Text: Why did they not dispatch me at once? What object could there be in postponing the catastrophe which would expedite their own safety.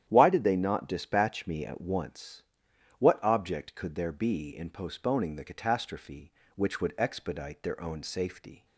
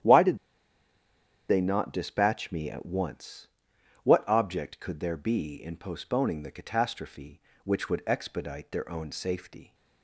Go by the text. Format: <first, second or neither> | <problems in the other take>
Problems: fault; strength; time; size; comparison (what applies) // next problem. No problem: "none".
first | starts louder than the rest; strong; until 2.1 s; 10.5 dB; strong in the first // pauses between "did" and "they"; at 0.3 s; 1.1 s long